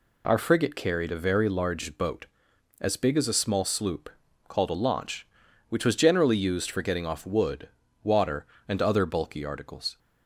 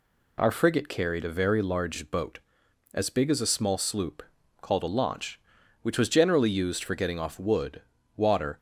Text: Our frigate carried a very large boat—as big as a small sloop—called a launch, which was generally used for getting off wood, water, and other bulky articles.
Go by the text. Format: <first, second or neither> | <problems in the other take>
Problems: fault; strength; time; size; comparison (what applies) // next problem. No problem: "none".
first | stops before "and other bulky articles"; at 8.5 s